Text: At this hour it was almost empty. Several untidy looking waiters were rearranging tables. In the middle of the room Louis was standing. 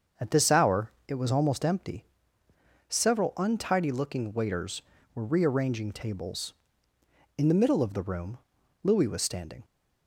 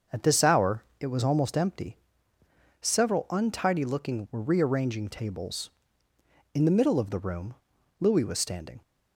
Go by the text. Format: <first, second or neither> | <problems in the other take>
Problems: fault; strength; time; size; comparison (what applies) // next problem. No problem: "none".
first | starts louder than the rest; until 1.2 s; 6.5 dB; also in the first // pauses between "hour" and "it"; slight; at 0.8 s; 0.16 s long; slight in the first // skips "waiters"; at 4.2 s // pauses between "room" and "Louis"; at 7.5 s; 0.44 s long; also in the first